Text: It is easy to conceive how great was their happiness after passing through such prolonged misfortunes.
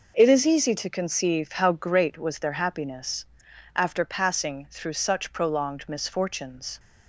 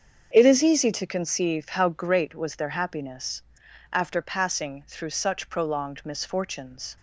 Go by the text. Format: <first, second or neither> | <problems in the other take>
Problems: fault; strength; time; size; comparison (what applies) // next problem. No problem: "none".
first | starts louder than the rest; strong; until 1.4 s; 7 dB // pauses between "happiness" and "after"; noticeable; at 3.4 s; 0.50 s long; noticeable in the first